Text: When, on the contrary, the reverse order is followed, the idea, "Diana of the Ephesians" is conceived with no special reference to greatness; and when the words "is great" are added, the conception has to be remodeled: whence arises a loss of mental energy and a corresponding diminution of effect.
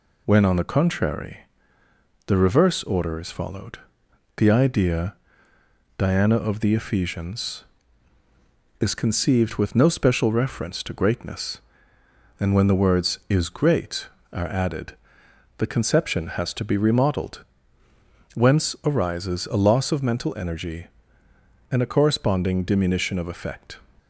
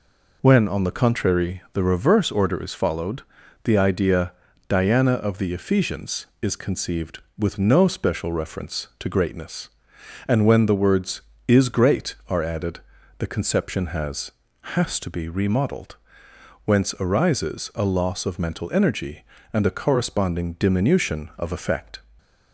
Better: first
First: none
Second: says "has" twice; at 14.7 s

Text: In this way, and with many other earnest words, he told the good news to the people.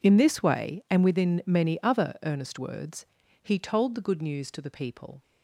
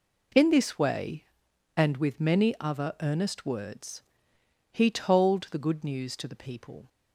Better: second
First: says "within" for "with"; at 1.0 s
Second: none

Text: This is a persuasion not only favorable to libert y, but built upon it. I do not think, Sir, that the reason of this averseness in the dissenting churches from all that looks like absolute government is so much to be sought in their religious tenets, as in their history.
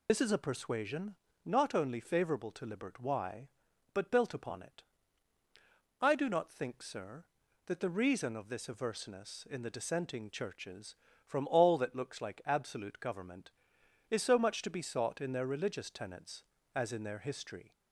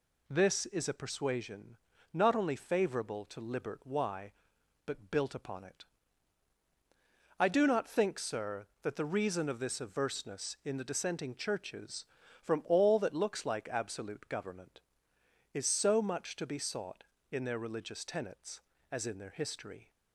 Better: second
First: loses the start of "This"; at 0.0 s; 65 ms // pauses between "persuasion" and "not"; slight; at 1.1 s; 0.30 s long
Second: pauses between "persuasion" and "not"; slight; at 1.7 s; 0.36 s long

